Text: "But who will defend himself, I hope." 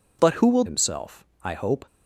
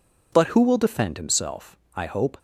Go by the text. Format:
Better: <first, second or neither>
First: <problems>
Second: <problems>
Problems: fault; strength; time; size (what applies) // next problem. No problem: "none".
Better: second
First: skips "defend"; at 0.6 s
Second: none